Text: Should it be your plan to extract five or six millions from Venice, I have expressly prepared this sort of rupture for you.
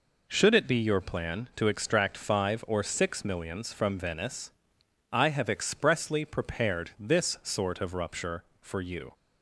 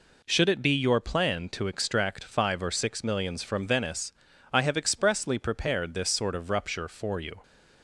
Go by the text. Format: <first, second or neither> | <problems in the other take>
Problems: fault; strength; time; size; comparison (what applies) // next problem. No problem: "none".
neither | none